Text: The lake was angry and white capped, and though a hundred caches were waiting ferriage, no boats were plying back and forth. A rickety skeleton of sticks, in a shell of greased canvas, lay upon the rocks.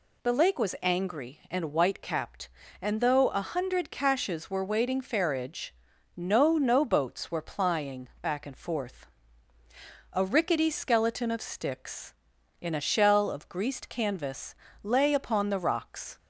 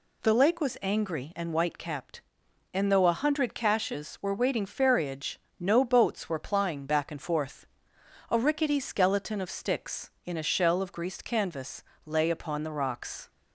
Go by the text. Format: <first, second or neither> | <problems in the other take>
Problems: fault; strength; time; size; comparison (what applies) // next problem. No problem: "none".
second | says "no" twice; at 6.5 s